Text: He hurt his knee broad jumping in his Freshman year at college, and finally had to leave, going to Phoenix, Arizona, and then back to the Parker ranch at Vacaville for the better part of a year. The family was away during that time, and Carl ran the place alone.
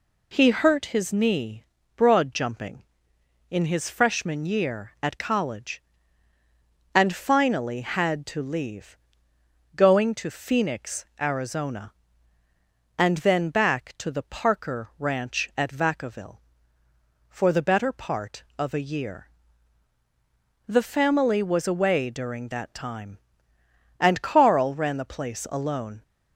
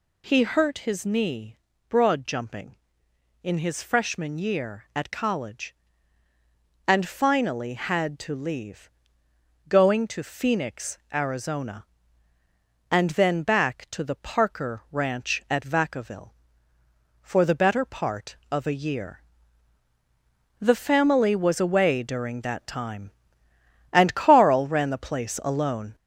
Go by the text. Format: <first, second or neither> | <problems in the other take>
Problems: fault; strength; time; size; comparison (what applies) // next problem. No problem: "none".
first | gets louder; throughout; 3.5 dB // pauses between "knee" and "broad"; slight; at 1.5 s; 0.32 s long; slight in the first